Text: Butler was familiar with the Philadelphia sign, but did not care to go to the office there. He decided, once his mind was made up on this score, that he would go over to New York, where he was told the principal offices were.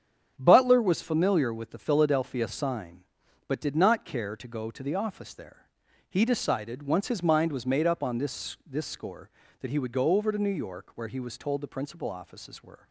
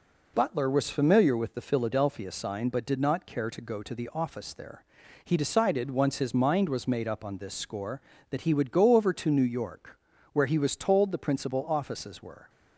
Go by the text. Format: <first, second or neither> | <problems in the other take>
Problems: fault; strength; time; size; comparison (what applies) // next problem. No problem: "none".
second | starts louder than the rest; strong; until 1.3 s; 8 dB // says "this" twice; at 8.6 s